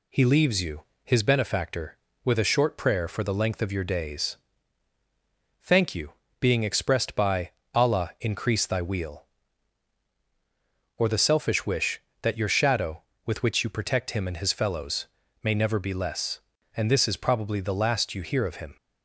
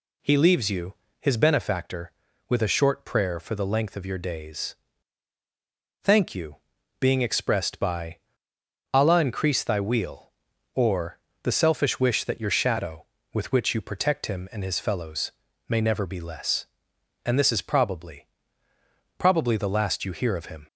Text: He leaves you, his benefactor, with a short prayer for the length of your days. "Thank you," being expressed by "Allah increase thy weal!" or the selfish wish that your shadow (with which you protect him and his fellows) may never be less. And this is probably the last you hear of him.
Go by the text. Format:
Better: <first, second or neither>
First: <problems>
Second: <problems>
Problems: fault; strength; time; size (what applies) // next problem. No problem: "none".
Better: first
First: pauses between "by" and "Allah"; slight; at 7.5 s; 0.24 s long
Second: pauses between "by" and "Allah"; noticeable; at 8.1 s; 0.76 s long // pauses between "or" and "the"; slight; at 11.1 s; 0.24 s long // says "probably" twice; at 19.1 s